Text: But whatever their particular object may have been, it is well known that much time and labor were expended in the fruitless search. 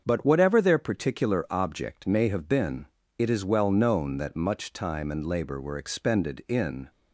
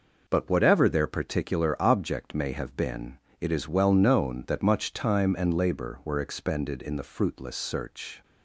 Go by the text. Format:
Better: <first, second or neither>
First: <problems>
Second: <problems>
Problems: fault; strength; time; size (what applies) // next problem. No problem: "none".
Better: second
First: starts louder than the rest; until 1.0 s; 7 dB // stops before "the fruitless search"; at 6.8 s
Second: none